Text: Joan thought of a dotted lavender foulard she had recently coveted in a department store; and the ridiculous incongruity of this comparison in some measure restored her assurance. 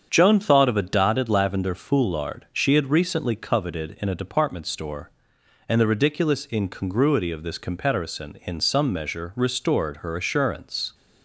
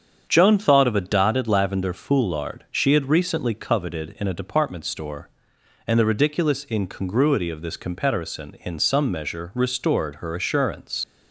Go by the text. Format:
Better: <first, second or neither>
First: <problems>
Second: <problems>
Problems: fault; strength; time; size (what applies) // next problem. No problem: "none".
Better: first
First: starts louder than the rest; strong; until 1.1 s; 7.5 dB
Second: starts louder than the rest; strong; until 1.2 s; 7.5 dB // leaves "assurance" unfinished; at 11.0 s; 90 ms